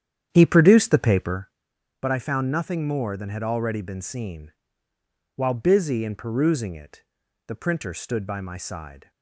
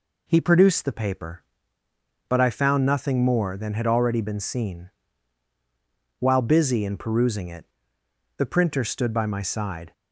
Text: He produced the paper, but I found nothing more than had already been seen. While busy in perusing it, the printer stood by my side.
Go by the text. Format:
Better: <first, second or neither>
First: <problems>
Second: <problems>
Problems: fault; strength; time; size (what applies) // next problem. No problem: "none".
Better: second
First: starts louder than the rest; strong; until 1.4 s; 9.5 dB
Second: none